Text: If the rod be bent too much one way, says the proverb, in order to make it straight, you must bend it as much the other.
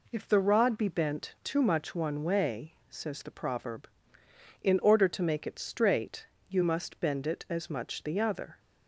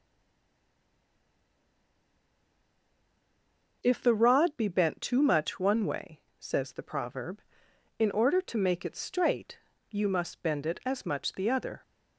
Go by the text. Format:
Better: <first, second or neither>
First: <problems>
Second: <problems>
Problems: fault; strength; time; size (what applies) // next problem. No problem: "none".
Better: first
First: none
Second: stays silent before the first word; strong; until 3.8 s; 3.8 s long